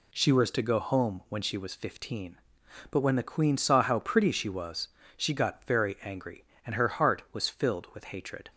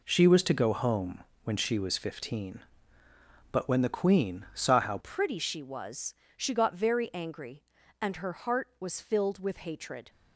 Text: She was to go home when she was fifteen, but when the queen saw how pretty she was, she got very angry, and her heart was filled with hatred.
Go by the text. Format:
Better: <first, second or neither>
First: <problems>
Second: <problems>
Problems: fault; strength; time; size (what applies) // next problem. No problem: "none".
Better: first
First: none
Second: pauses between "home" and "when"; slight; at 1.2 s; 0.22 s long // changes voice at "pretty"; from 4.9 s on; 5.1 s long